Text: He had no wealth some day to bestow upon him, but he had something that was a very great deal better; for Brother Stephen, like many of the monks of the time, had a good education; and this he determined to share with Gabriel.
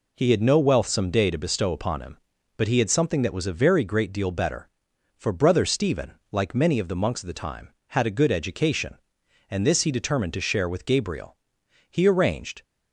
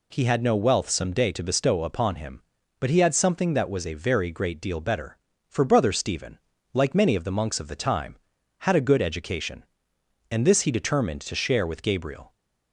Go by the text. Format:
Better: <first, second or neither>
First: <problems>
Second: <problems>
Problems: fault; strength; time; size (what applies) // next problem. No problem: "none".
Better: second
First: goes on to say "He arranged"; noticeable; from 11.9 s on; 0.72 s long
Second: none